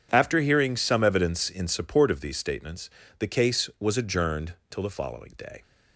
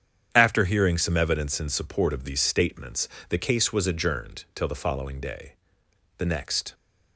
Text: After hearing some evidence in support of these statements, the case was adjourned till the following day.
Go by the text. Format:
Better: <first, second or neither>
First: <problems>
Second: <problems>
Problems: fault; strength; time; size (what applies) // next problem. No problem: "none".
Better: first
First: none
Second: starts louder than the rest; strong; until 1.3 s; 8.5 dB // goes on to say "The next"; from 6.1 s on; 0.56 s long